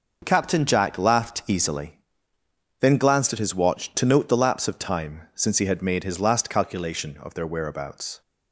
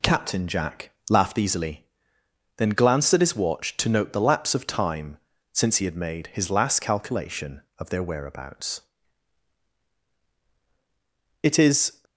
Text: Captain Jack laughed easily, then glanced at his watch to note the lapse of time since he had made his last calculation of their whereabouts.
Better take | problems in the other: first | pauses between "Jack" and "laughed"; slight; at 0.8 s; 0.20 s long // pauses between "time" and "since"; slight; at 5.1 s; 0.34 s long // goes on to say "It is"; from 11.4 s on; 0.60 s long

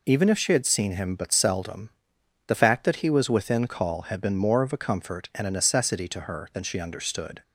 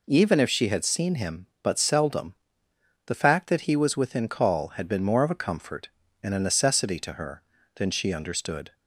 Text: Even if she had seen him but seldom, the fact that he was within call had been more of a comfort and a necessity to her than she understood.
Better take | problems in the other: neither | none

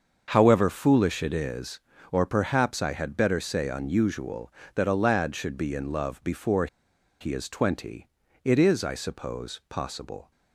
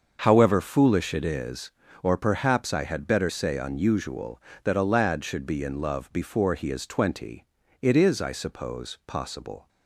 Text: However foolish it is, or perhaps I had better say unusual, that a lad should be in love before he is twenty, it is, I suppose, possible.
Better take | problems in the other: second | starts louder than the rest; until 1.2 s; 6.5 dB; also in the second // pauses between "before" and "he"; noticeable; at 6.6 s; 0.53 s long

